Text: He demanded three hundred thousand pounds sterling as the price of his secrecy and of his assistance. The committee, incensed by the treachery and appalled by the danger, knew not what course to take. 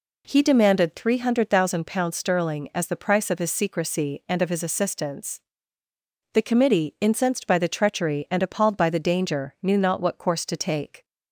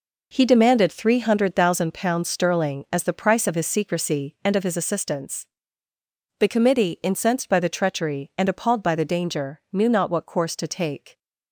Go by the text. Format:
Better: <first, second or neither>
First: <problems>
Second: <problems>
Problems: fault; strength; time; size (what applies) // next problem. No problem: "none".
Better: first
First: none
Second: gets quieter; strong; throughout; 9.5 dB